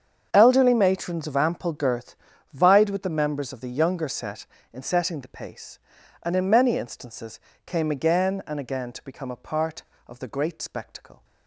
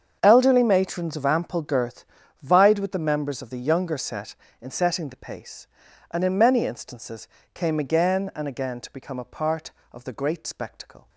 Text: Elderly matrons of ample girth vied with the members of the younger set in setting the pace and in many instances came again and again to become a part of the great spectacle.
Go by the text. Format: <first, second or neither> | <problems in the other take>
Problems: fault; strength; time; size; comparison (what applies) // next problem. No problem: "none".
neither | starts louder than the rest; strong; the same in both // pauses between "girth" and "vied"; the same in both // pauses between "instances" and "came"; slight; the same in both